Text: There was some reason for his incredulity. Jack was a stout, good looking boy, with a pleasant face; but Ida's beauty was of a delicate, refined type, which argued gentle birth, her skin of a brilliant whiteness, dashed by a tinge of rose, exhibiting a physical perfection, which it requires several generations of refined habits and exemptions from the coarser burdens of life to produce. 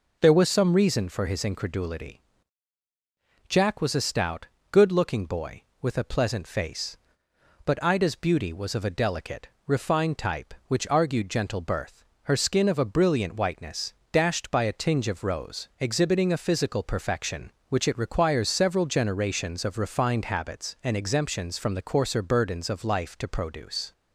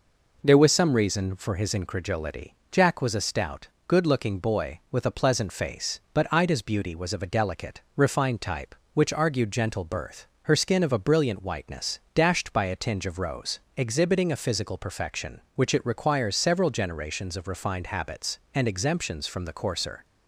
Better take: first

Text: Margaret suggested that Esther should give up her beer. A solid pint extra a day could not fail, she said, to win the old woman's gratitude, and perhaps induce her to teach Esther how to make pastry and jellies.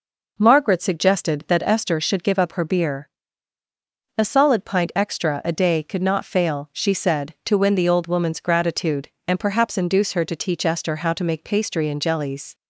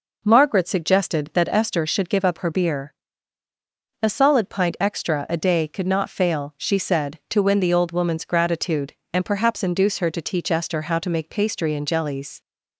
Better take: neither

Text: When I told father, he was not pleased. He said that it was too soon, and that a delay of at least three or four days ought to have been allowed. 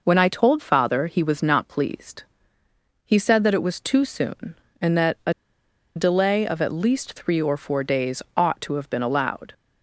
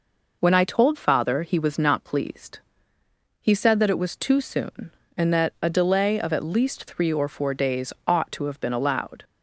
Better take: second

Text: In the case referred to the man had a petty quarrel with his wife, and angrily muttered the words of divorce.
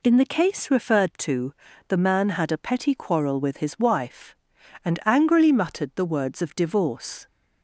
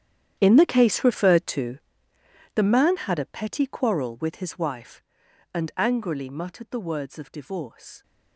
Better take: first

